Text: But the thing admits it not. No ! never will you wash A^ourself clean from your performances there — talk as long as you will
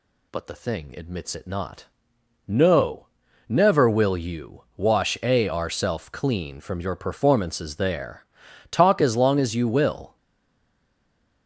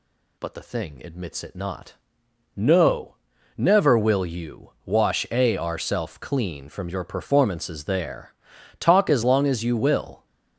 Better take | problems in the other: second | stays silent after the last word; noticeable; from 10.1 s on; 1.3 s long

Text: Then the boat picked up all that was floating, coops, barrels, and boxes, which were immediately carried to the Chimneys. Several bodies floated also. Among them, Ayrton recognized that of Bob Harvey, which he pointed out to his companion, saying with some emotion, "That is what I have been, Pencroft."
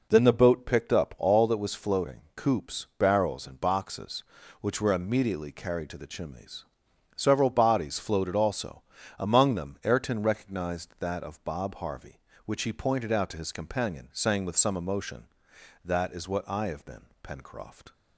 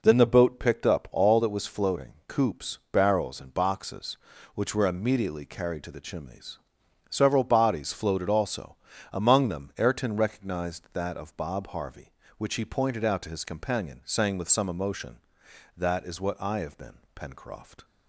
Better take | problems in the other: neither | none

